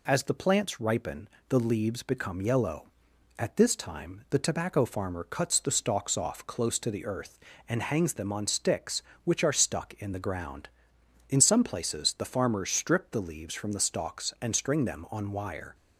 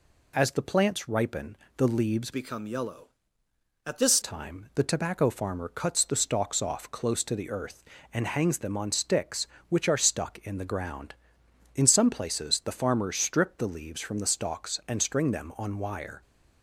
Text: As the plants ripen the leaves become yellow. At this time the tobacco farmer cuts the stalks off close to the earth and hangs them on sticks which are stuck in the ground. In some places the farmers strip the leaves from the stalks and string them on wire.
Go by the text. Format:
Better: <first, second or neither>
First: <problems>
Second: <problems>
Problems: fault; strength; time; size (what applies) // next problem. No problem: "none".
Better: first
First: pauses between "ripen" and "the"; slight; at 1.2 s; 0.20 s long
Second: pauses between "ripen" and "the"; slight; at 1.5 s; 0.20 s long // changes voice from "become" to "this"; from 2.3 to 4.1 s; 1.8 s long